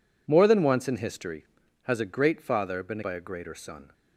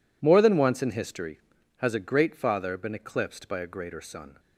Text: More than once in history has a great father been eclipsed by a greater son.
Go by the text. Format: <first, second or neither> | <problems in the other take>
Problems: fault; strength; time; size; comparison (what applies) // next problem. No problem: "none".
second | skips "eclipsed"; at 3.0 s